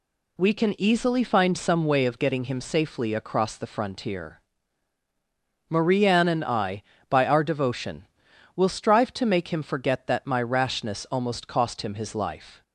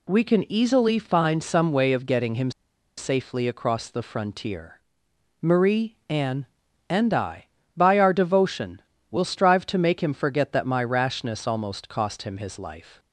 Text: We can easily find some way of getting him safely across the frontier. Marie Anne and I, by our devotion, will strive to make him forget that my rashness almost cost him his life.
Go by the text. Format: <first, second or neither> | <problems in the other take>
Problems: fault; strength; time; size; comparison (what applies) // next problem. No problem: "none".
first | pauses between "him" and "safely"; noticeable; at 2.5 s; 0.47 s long